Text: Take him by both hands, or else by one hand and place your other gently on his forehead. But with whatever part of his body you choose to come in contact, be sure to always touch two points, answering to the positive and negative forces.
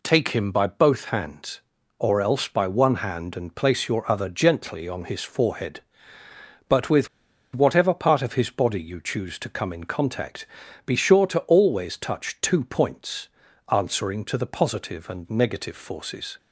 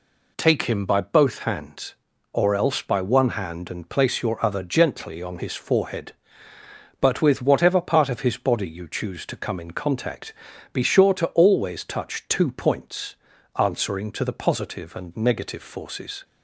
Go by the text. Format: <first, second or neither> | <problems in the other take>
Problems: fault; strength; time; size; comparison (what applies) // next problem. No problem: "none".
second | pauses between "with" and "whatever"; noticeable; at 7.0 s; 0.47 s long